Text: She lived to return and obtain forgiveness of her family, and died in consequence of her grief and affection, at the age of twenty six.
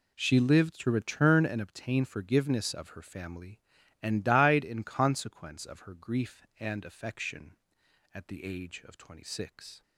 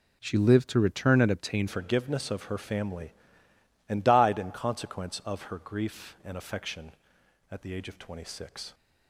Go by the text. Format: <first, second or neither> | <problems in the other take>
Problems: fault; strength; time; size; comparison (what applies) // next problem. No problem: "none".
first | changes voice at "forgiveness"; from 1.6 s on; 7.1 s long